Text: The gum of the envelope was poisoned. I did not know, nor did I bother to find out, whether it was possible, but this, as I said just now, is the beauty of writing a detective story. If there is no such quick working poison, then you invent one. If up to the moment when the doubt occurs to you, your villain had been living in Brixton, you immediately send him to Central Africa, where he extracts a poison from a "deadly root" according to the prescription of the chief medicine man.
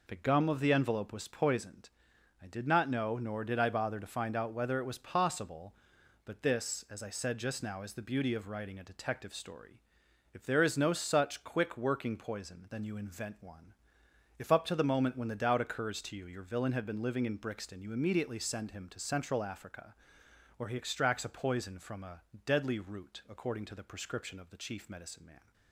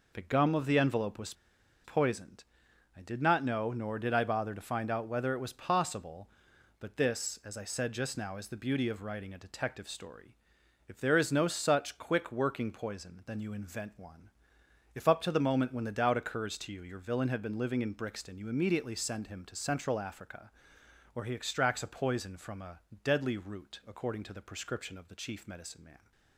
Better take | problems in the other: first | pauses between "was" and "poisoned"; noticeable; at 1.3 s; 0.51 s long // pauses between "a" and "deadly"; slight; at 22.7 s; 0.24 s long; slight in the first

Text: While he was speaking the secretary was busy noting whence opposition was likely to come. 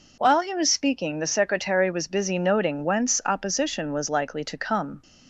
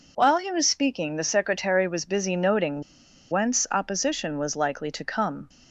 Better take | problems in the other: first | pauses between "noting" and "whence"; noticeable; at 2.8 s; 0.50 s long

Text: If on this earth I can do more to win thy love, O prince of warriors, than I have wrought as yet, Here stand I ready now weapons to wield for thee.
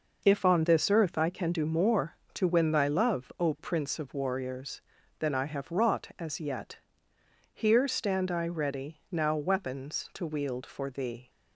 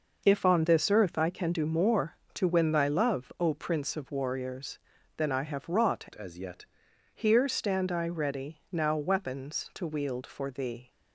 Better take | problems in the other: first | changes voice from "as" to "yet"; from 6.1 to 6.6 s; 0.5 s long

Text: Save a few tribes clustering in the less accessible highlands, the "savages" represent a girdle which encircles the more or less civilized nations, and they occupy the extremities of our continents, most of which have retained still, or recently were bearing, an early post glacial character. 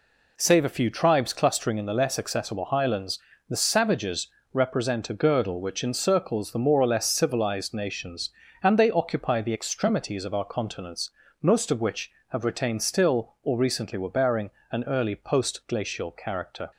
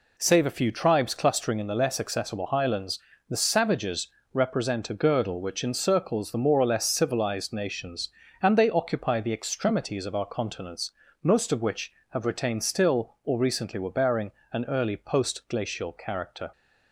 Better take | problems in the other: neither | pauses between "savages" and "represent"; slight; the same in both

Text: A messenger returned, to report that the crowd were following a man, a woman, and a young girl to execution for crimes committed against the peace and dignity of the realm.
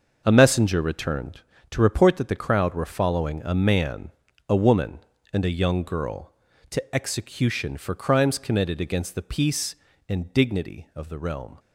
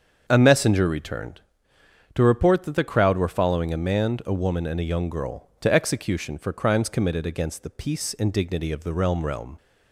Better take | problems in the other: first | starts louder than the rest; until 1.2 s; 7 dB // says "realm" twice; at 9.2 s

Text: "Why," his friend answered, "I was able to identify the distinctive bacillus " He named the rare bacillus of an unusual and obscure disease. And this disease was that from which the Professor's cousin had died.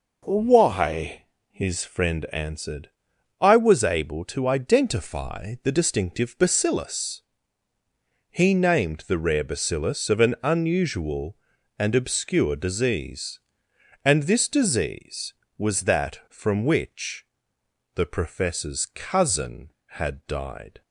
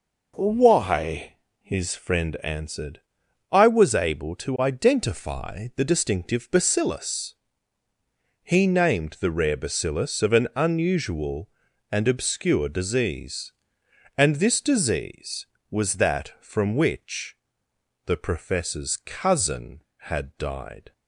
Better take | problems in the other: neither | pauses between "which" and "the"; noticeable; the same in both

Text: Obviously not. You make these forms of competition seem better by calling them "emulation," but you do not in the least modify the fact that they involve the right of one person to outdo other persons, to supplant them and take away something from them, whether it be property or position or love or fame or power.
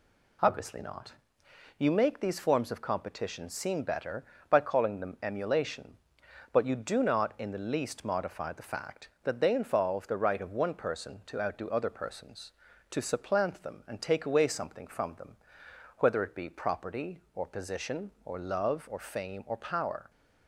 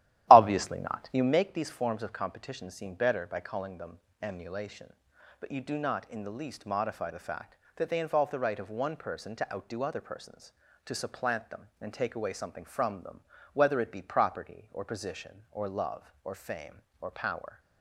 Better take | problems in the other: first | starts louder than the rest; strong; until 1.4 s; 14 dB // pauses between "them" and "emulation"; slight; at 3.9 s; 0.24 s long

